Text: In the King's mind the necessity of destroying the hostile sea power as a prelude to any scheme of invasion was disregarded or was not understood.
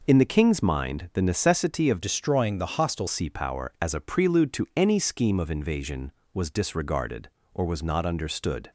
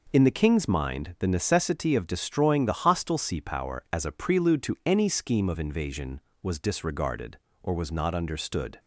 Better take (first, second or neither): second